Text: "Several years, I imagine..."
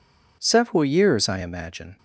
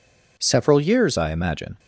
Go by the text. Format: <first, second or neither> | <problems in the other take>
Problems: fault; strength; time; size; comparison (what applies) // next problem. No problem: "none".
first | changes voice at "I"; from 1.1 s on; 0.6 s long